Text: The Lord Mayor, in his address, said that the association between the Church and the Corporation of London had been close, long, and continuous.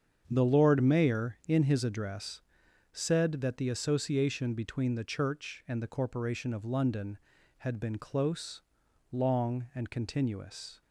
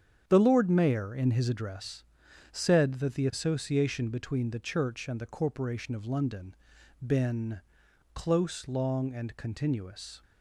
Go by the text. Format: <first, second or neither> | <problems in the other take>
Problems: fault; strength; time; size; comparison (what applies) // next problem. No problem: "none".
first | starts louder than the rest; strong; until 1.2 s; 8.5 dB; strong in the first // skips "had"; at 6.7 s // pauses between "been" and "close"; noticeable; at 7.6 s; 0.52 s long